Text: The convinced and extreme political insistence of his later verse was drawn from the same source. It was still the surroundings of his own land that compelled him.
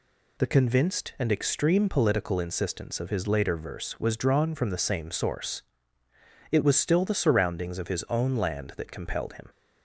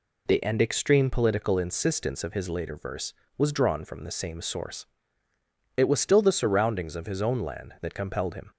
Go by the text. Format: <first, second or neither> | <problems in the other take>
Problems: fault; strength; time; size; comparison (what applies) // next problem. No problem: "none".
first | skips "convinced"; at 0.4 s